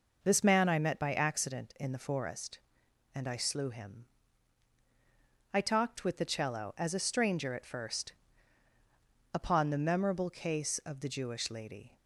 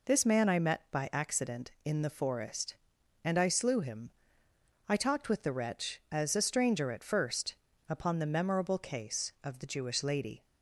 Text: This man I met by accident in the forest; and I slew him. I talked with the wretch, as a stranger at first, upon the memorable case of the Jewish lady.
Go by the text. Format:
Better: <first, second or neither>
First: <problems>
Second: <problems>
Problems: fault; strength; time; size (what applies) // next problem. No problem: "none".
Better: second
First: says "cello" for "wretch"; at 6.2 s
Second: none